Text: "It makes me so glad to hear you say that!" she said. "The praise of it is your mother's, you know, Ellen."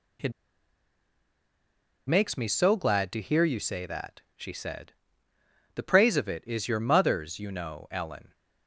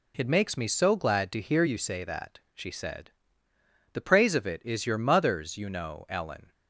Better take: second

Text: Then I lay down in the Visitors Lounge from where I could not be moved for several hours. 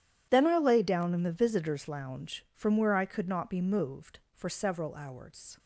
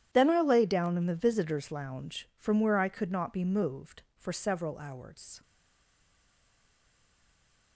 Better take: first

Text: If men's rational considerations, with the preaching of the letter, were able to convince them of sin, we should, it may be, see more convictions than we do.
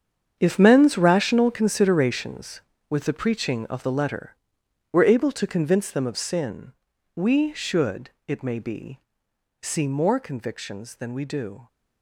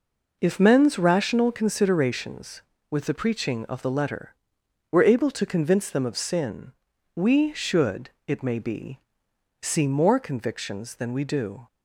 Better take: second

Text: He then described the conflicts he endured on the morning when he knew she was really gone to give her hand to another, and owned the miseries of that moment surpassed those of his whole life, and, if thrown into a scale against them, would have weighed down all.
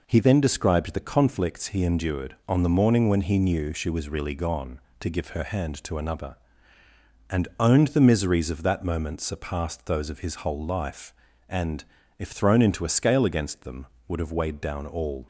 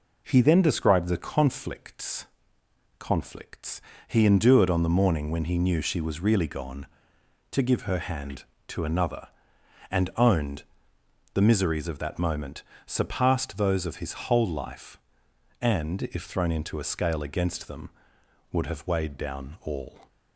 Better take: first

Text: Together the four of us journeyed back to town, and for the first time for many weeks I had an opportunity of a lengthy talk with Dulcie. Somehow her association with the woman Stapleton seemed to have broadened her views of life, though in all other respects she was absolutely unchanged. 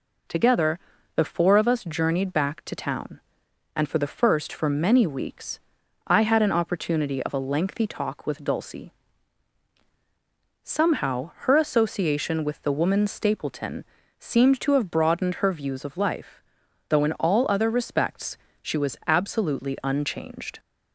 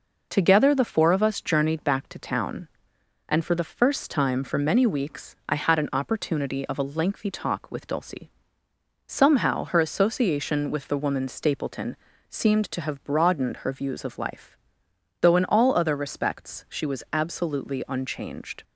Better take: second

